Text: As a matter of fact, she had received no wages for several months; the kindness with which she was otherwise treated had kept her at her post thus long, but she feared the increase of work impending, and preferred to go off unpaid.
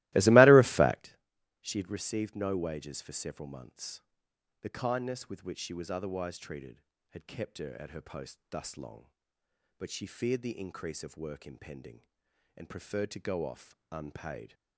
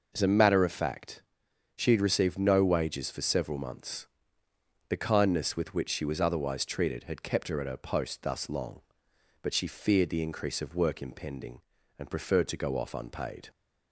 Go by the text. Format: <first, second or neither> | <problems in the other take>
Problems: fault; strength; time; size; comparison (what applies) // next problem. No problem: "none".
second | starts louder than the rest; strong; until 1.1 s; 18.5 dB // pauses between "off" and "unpaid"; slight; at 13.7 s; 0.16 s long